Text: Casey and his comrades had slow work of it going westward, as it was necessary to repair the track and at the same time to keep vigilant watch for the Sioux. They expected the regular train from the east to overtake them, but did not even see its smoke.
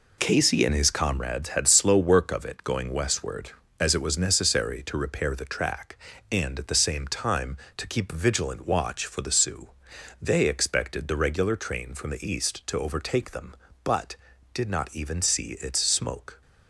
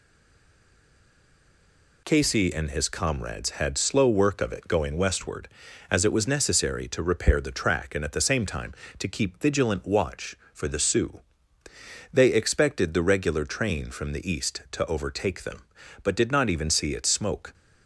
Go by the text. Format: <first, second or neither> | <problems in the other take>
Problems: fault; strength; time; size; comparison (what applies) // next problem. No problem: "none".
first | stays silent before the first word; noticeable; until 2.0 s; 2.0 s long